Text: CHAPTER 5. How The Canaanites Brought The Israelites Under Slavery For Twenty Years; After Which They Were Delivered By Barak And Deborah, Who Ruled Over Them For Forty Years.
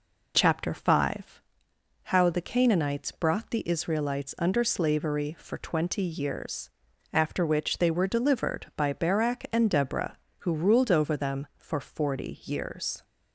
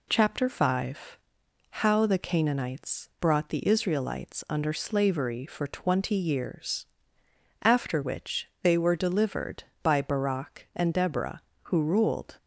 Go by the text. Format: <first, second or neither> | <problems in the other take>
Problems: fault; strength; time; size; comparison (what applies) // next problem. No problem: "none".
first | stops before "Over Them For Forty Years"; at 12.3 s